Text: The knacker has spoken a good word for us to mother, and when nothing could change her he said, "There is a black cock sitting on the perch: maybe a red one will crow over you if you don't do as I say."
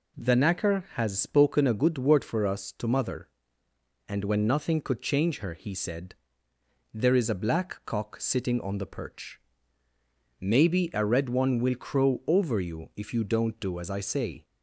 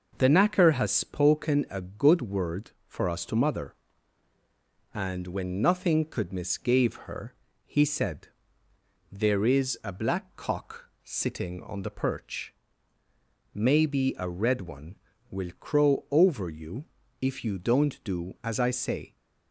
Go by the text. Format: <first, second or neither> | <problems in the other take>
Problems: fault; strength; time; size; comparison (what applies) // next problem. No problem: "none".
first | says "misgave" for "change"; at 6.3 s // pauses between "her" and "he"; slight; at 7.3 s; 0.32 s long // pauses between "you" and "if"; slight; at 16.8 s; 0.36 s long